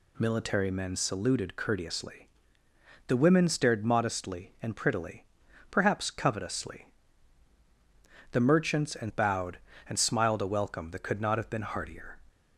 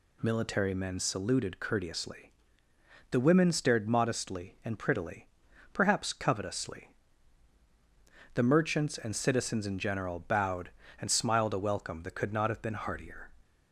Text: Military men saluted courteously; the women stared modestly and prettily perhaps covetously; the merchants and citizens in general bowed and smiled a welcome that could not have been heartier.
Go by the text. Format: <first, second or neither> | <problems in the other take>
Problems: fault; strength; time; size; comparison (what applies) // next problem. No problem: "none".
second | pauses between "prettily" and "perhaps"; at 5.2 s; 0.44 s long; also in the second // skips "citizens in general"; at 9.0 s